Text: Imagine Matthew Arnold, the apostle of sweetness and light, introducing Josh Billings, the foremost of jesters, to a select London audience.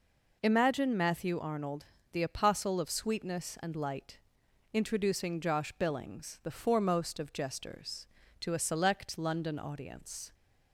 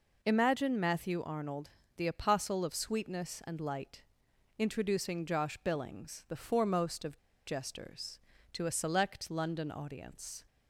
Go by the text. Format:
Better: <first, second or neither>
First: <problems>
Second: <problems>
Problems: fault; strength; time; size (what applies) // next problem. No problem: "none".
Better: first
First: none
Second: pauses between "of" and "jesters"; slight; at 7.1 s; 0.28 s long